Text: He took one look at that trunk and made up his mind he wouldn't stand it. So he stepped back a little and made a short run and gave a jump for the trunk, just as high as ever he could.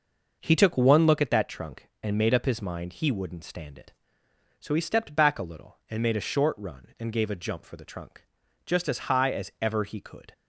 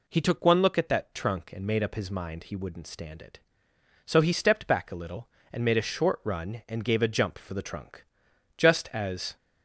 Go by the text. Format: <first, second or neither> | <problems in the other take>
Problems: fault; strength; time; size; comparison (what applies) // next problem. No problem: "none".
first | stops before "high as ever he could"; at 9.3 s